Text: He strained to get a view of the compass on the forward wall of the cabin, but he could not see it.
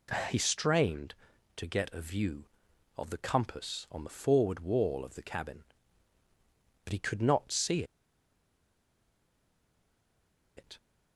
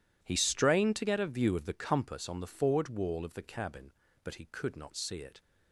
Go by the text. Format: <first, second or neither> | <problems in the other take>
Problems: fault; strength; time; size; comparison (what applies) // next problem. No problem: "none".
second | pauses between "see" and "it"; strong; at 7.8 s; 2.7 s long